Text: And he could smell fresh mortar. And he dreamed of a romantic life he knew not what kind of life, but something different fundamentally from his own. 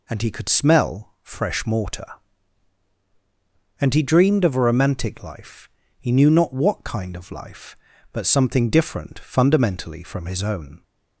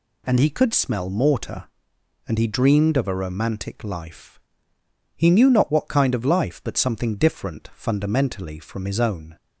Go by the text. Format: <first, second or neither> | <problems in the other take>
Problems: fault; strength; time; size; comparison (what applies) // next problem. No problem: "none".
first | skips "fresh"; at 1.0 s // pauses between "life" and "he"; noticeable; at 4.3 s; 0.78 s long; slight in the first